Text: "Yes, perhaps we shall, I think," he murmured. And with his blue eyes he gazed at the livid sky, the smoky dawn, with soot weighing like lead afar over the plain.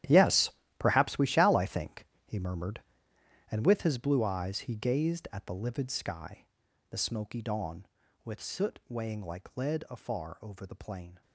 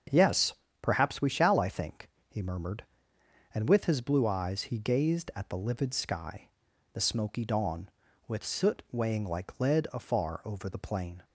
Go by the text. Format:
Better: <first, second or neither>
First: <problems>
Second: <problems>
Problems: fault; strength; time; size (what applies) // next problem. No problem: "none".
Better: second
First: gets quieter; strong; throughout; 15 dB // starts louder than the rest; strong; until 1.3 s; 11.5 dB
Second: starts louder than the rest; until 1.3 s; 7 dB